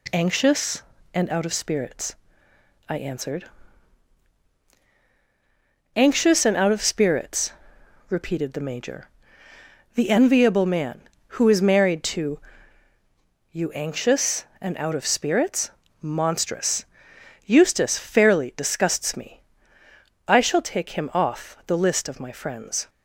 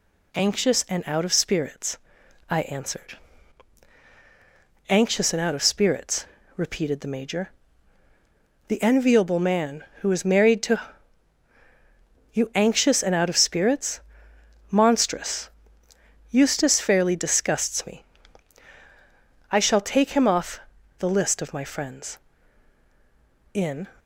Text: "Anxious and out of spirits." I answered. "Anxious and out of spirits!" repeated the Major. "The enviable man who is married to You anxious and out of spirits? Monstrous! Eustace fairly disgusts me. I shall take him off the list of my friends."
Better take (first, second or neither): first